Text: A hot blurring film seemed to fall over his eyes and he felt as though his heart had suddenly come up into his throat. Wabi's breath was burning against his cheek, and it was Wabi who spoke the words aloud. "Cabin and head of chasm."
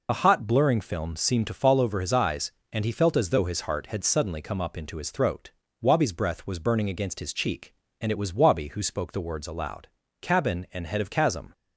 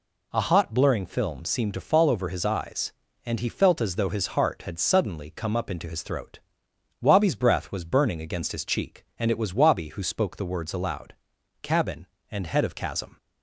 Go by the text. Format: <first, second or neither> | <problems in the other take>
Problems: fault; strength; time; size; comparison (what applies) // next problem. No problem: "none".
second | loses the start of "A"; at 0.0 s; 40 ms